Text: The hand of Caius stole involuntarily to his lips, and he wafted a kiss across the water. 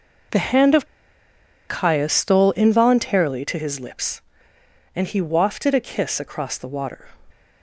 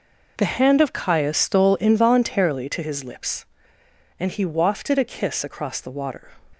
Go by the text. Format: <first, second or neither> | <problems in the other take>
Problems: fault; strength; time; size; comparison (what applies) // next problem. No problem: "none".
second | pauses between "of" and "Caius"; noticeable; at 0.8 s; 0.82 s long